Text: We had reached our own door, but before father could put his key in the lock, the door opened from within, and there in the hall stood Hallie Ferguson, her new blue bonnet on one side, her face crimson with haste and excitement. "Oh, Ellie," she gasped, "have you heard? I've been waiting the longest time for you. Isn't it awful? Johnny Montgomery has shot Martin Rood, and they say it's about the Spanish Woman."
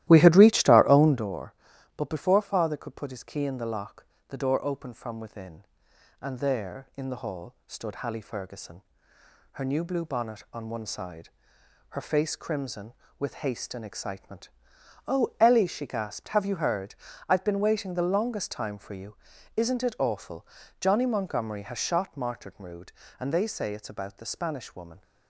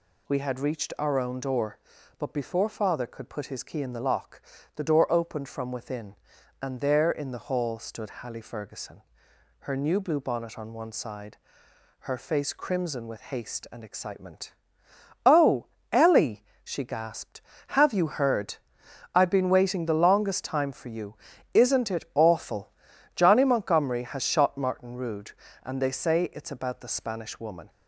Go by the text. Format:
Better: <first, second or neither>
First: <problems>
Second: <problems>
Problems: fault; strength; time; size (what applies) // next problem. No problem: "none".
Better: second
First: starts louder than the rest; strong; until 1.4 s; 14.5 dB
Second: none